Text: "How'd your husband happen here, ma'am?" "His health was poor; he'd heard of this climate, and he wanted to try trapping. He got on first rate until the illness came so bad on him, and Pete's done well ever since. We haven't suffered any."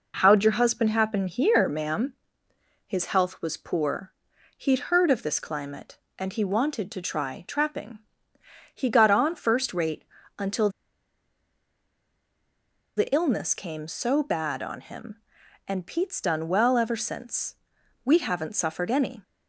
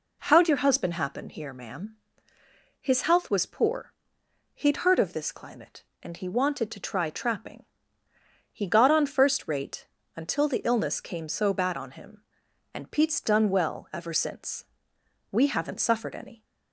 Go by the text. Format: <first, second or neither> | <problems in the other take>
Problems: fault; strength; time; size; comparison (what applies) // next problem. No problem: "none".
second | pauses between "rate" and "until"; slight; at 10.0 s; 0.34 s long; slight in the second // pauses between "until" and "the"; strong; at 10.6 s; 2.2 s long